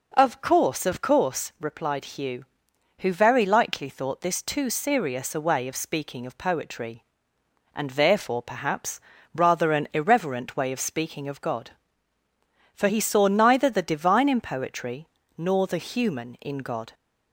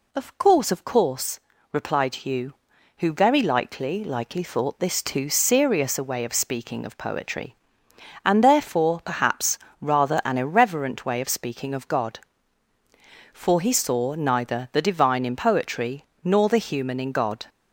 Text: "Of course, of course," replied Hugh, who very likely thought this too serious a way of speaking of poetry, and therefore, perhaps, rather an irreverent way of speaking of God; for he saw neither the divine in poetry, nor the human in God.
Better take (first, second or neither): first